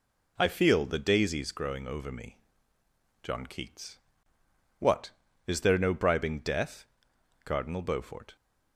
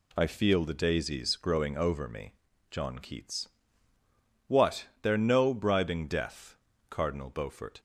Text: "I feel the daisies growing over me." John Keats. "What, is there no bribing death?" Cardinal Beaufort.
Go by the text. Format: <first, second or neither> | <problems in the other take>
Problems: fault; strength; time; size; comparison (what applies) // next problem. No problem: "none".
first | skips "is"; at 4.9 s